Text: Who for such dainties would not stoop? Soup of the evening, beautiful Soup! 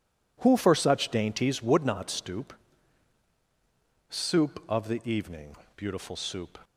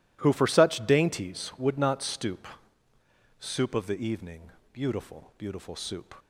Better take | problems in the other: first | says "beautiful" twice; at 5.3 s

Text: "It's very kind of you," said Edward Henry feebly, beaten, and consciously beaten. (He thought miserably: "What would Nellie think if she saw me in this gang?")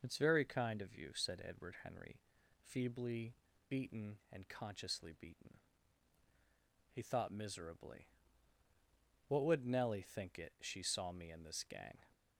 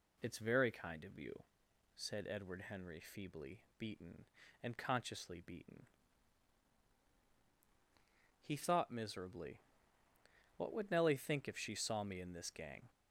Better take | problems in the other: second | pauses between "Henry" and "feebly"; at 2.2 s; 0.42 s long // says "it" for "if"; at 10.3 s

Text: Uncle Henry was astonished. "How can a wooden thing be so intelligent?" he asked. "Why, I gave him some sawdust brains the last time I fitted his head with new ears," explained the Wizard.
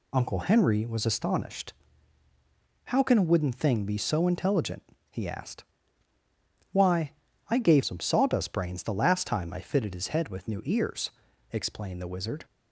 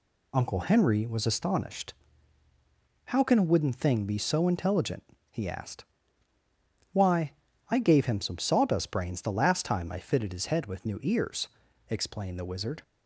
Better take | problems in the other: second | skips "him"; at 7.8 s

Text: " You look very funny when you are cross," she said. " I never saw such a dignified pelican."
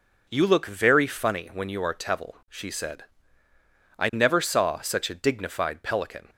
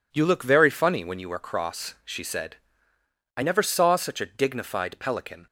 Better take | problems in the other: second | says "tevil" for "cross"; at 1.9 s

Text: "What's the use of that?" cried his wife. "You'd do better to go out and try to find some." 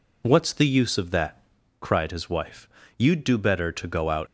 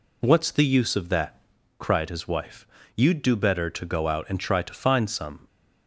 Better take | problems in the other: second | stops before "and try to find some"; at 4.2 s

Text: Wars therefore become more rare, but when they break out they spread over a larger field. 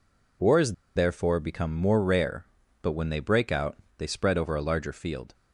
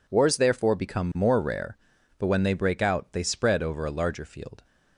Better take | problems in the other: second | pauses between "Wars" and "therefore"; slight; at 0.7 s; 0.23 s long // pauses between "out" and "they"; slight; at 3.7 s; 0.22 s long

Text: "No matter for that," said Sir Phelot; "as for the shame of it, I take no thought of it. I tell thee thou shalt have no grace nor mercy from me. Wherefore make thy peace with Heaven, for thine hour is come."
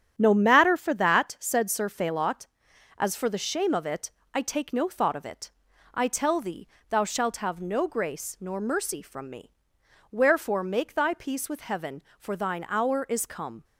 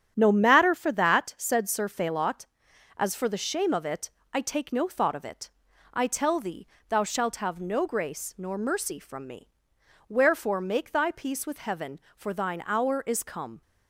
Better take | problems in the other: neither | starts louder than the rest; strong; the same in both // pauses between "thee" and "thou"; slight; the same in both

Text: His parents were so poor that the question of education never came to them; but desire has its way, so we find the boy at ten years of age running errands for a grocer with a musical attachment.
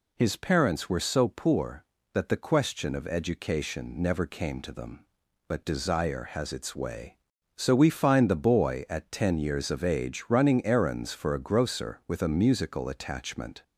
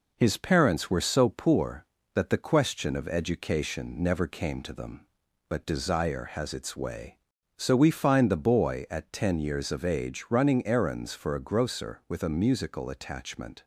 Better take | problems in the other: first | gets quieter; slight; throughout; 2.5 dB

